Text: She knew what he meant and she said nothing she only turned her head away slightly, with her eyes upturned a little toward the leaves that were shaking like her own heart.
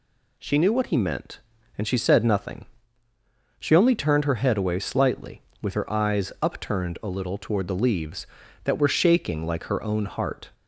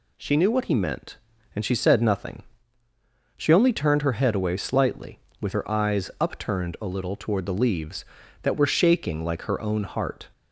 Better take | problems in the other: neither | pauses between "nothing" and "she"; noticeable; the same in both

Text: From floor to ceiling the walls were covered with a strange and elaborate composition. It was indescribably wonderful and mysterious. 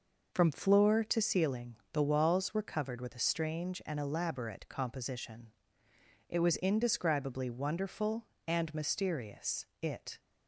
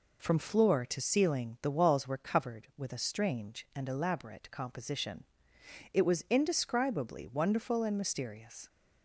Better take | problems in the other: second | pauses between "ceiling" and "the"; slight; at 1.7 s; 0.16 s long // goes on to say "It"; slight; from 9.8 s on; 0.38 s long

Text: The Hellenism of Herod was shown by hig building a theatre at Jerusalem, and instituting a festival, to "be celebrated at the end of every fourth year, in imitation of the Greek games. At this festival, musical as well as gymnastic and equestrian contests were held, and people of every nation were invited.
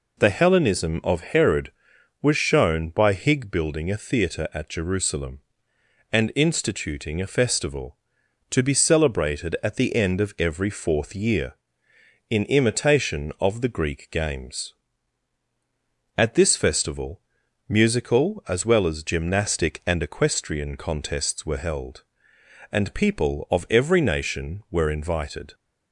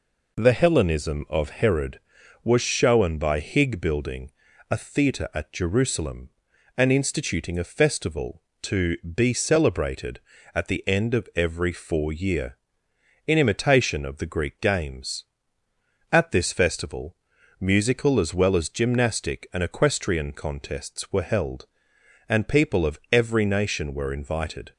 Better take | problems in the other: first | pauses between "building" and "a"; at 4.3 s; 0.40 s long // says "four" for "fourth"; at 11.7 s

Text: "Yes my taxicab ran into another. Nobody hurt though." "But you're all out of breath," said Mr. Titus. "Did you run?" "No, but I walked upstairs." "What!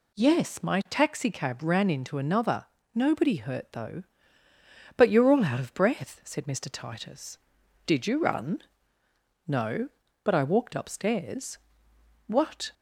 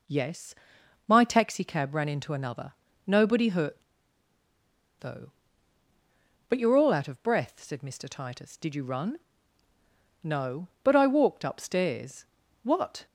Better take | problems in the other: first | pauses between "Yes" and "my"; noticeable; at 0.5 s; 0.54 s long // pauses between "hurt" and "though"; at 3.8 s; 1.1 s long

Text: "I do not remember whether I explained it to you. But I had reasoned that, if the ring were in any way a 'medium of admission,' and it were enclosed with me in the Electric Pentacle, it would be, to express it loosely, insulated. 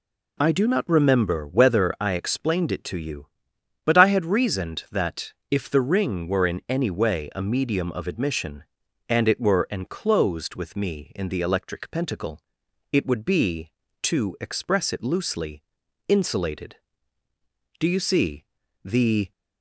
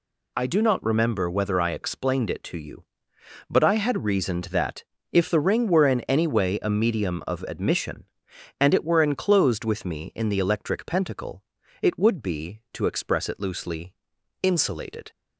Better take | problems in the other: second | goes on to say "Do you see The"; from 17.7 s on; 1.5 s long

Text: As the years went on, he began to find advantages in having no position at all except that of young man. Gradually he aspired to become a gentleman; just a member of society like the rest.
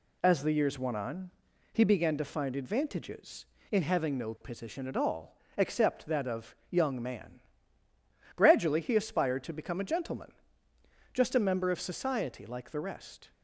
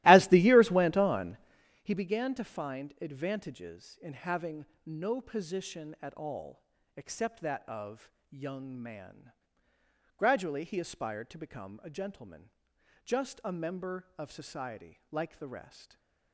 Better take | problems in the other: first | starts louder than the rest; strong; until 1.7 s; 17.5 dB // pauses between "having" and "no"; slight; at 4.6 s; 0.18 s long // pauses between "all" and "except"; slight; at 6.6 s; 0.34 s long; slight in the first // pauses between "of" and "young"; slight; at 8.1 s; 0.20 s long; slight in the first // stays silent after the last word; slight; from 15.8 s on; 0.5 s long

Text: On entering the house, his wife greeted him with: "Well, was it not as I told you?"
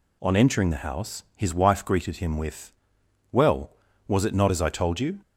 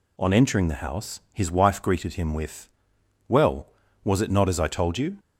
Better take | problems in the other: neither | none

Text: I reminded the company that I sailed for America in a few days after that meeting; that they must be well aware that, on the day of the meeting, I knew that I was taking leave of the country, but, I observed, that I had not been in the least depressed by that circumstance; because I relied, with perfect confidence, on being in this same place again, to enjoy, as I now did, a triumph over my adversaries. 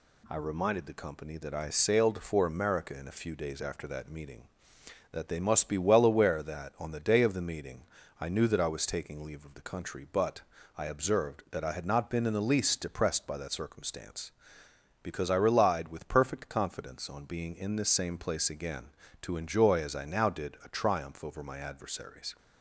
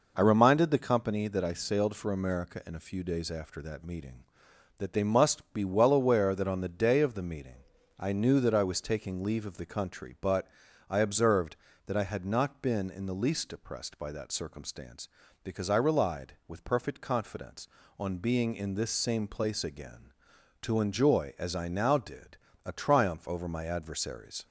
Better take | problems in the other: neither | none

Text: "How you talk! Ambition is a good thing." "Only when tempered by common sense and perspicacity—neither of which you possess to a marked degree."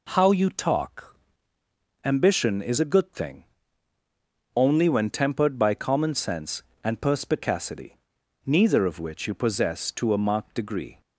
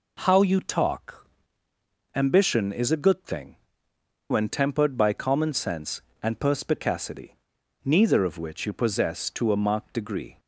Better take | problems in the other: first | skips "Only"; at 3.9 s

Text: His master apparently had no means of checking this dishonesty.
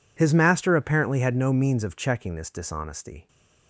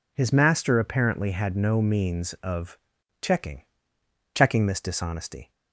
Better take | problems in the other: first | pauses between "of" and "checking"; at 2.7 s; 0.44 s long // says "checking" twice; at 4.3 s

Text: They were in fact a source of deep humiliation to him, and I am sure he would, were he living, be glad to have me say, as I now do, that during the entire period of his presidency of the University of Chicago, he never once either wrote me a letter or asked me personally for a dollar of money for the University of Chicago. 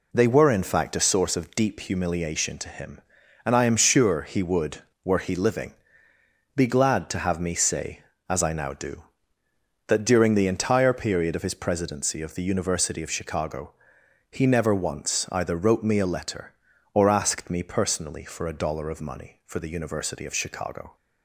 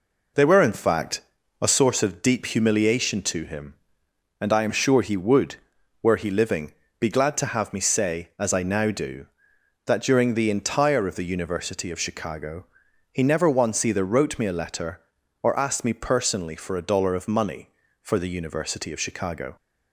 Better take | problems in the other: first | pauses between "fact" and "a"; at 1.2 s; 0.40 s long // skips "period of his presidency"; at 11.0 s

